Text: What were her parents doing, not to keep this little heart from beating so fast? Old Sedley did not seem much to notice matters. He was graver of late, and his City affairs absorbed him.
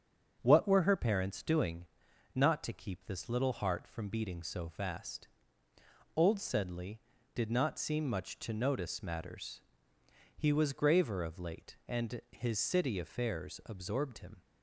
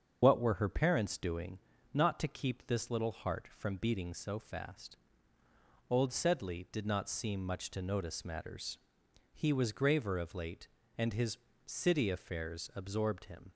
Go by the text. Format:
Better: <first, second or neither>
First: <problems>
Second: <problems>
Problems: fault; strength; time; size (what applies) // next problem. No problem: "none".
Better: first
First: starts louder than the rest; until 1.4 s; 7 dB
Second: loses the start of "What"; at 0.2 s; 55 ms // starts louder than the rest; until 1.2 s; 7 dB // pauses between "his" and "City"; slight; at 11.3 s; 0.30 s long